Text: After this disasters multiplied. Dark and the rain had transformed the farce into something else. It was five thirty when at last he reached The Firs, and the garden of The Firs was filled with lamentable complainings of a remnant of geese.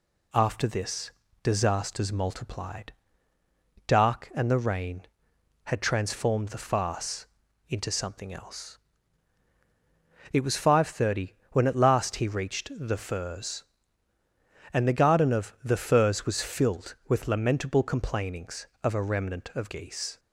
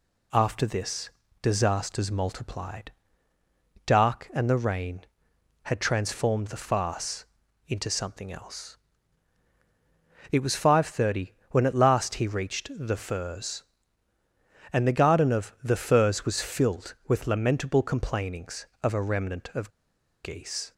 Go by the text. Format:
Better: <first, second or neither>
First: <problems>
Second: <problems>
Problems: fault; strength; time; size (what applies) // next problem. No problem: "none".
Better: first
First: pauses between "this" and "disasters"; slight; at 1.0 s; 0.32 s long // pauses between "farce" and "into"; at 7.2 s; 0.42 s long // pauses between "thirty" and "when"; slight; at 11.3 s; 0.20 s long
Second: pauses between "this" and "disasters"; slight; at 1.0 s; 0.32 s long // pauses between "farce" and "into"; at 7.2 s; 0.42 s long // pauses between "thirty" and "when"; slight; at 11.3 s; 0.20 s long // pauses between "of" and "geese"; noticeable; at 19.7 s; 0.53 s long